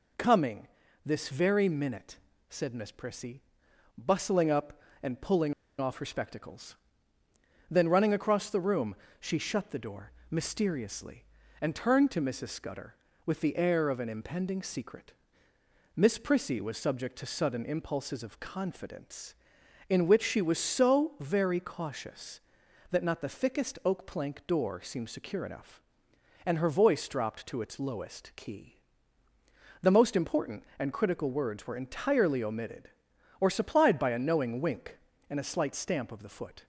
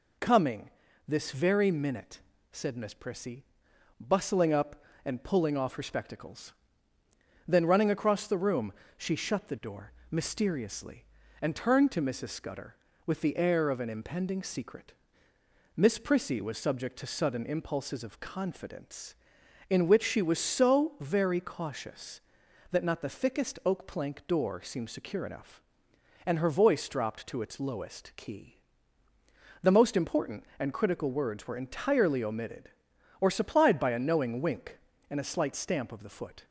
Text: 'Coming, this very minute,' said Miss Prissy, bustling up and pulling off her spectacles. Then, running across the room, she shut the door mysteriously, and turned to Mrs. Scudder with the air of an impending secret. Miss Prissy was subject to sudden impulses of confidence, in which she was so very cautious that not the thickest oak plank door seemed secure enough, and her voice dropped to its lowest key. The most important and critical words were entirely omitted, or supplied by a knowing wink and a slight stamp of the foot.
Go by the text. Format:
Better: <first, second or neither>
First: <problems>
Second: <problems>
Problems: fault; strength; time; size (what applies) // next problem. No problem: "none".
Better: second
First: pauses between "pulling" and "off"; slight; at 5.5 s; 0.25 s long // pauses between "door" and "mysteriously"; slight; at 10.1 s; 0.18 s long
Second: pauses between "door" and "mysteriously"; slight; at 9.9 s; 0.18 s long